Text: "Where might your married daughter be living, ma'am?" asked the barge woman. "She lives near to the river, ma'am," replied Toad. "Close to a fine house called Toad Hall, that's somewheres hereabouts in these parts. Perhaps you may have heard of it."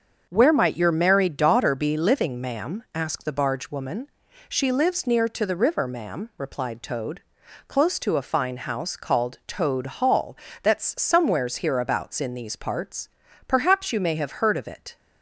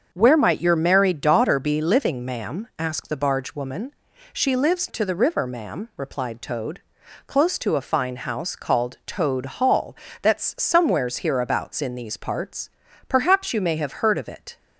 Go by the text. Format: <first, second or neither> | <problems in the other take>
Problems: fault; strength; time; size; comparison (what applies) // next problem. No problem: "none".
first | starts louder than the rest; until 1.1 s; 6.5 dB; also in the first // skips "near"; at 4.8 s